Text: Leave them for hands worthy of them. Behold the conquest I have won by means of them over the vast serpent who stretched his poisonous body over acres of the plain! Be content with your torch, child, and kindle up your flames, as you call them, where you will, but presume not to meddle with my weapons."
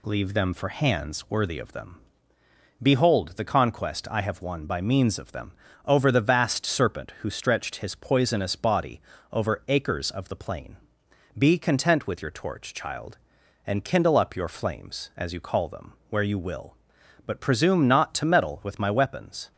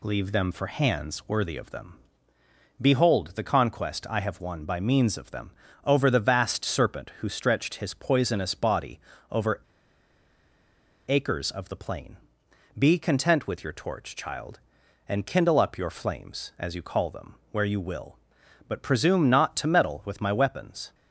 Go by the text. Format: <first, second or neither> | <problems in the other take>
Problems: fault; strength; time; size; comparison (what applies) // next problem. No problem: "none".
first | pauses between "them" and "over"; slight; at 5.5 s; 0.34 s long; slight in the first // pauses between "body" and "over"; slight; at 8.9 s; 0.32 s long; slight in the first // pauses between "over" and "acres"; strong; at 9.6 s; 1.4 s long